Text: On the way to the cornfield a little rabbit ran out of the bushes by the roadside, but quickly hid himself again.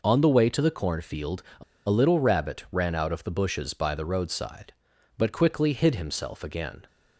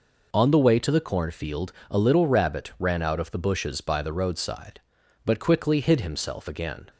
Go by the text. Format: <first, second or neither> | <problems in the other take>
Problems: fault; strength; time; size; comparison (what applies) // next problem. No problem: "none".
second | pauses between "cornfield" and "a"; slight; at 1.4 s; 0.16 s long; slight in the second // pauses between "a" and "little"; slight; at 1.6 s; 0.25 s long